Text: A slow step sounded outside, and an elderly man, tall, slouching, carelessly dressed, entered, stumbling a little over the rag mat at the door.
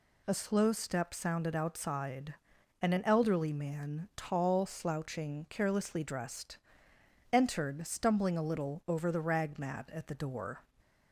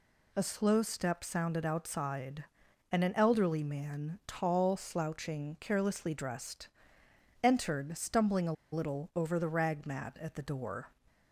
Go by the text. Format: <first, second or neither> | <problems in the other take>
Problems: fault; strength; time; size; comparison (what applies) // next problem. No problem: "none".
first | pauses between "a" and "little"; slight; at 8.5 s; 0.19 s long